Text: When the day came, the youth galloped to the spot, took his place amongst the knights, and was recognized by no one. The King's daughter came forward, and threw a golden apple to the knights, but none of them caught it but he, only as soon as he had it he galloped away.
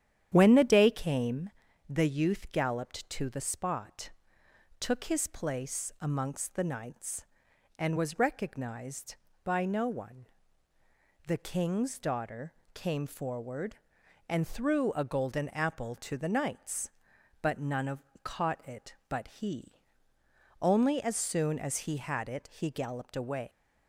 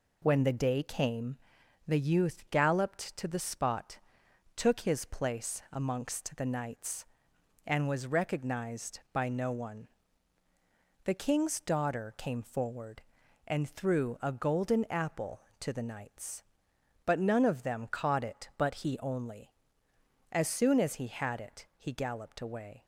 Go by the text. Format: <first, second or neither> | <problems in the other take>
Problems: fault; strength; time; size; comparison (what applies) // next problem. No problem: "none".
second | starts louder than the rest; strong; until 1.3 s; 10 dB // pauses between "daughter" and "came"; slight; at 12.5 s; 0.22 s long // skips "them"; at 18.0 s